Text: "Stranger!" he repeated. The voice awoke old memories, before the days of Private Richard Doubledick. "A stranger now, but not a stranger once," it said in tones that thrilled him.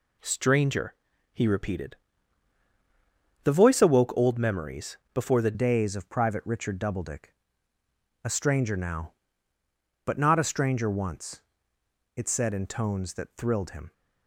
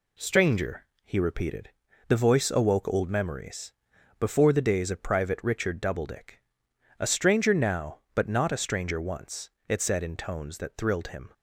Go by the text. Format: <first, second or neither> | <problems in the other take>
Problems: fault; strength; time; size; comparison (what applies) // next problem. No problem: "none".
second | changes voice at "days"; from 5.5 s on; 8.4 s long